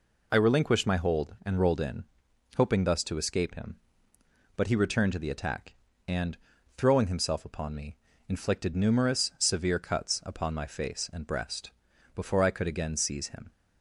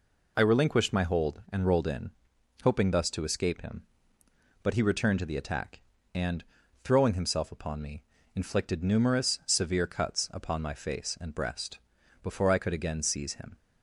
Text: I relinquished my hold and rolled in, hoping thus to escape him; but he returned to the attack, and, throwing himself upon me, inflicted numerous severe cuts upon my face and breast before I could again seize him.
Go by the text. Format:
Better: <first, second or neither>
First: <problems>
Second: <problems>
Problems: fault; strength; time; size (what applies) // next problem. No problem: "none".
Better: neither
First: pauses between "breast" and "before"; at 11.7 s; 0.42 s long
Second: pauses between "breast" and "before"; at 11.7 s; 0.42 s long